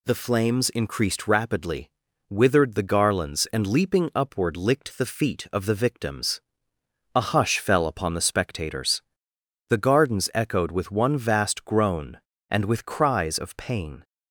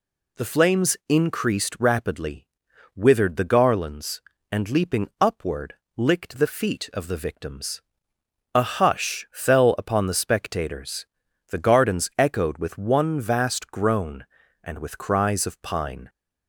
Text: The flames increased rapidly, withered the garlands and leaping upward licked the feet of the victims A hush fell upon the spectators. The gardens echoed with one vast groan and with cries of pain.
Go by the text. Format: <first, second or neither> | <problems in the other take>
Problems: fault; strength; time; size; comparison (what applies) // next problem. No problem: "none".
first | pauses between "upward" and "licked"; slight; at 5.7 s; 0.22 s long // pauses between "victims" and "A"; noticeable; at 7.8 s; 0.74 s long; noticeable in the first // says "pine" for "pain"; at 15.6 s